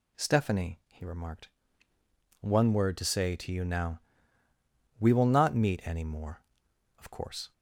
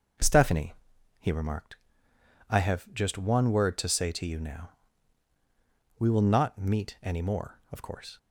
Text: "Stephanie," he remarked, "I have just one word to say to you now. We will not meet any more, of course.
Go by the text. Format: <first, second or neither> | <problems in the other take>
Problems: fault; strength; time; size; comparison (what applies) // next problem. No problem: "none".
second | skips "I have just"; at 1.9 s